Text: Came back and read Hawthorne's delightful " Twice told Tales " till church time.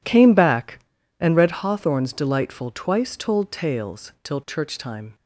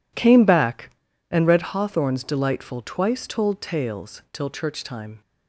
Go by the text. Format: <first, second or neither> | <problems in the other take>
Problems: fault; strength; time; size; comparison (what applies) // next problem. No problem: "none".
neither | none